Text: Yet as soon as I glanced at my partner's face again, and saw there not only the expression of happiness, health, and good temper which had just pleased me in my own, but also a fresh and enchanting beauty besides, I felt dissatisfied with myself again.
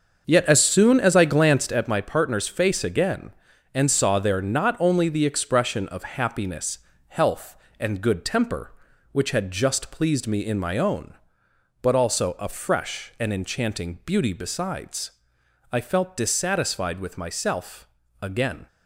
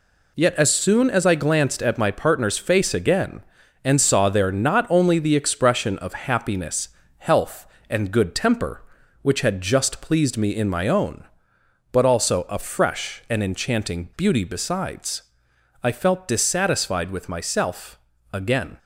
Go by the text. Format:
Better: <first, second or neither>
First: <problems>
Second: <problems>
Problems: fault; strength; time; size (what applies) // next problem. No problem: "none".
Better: second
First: starts louder than the rest; until 1.8 s; 6.5 dB // pauses between "myself" and "again"; slight; at 17.8 s; 0.34 s long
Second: pauses between "myself" and "again"; slight; at 17.9 s; 0.34 s long